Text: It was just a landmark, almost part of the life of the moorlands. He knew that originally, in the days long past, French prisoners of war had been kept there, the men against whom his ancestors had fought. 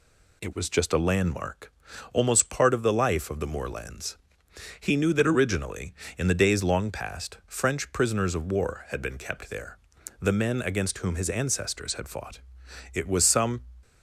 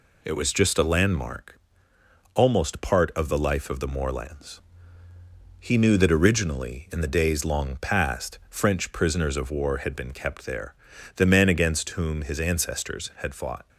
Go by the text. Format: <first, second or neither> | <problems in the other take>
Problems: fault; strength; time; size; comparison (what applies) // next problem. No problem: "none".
second | goes on to say "It was some"; noticeable; from 12.9 s on; 0.68 s long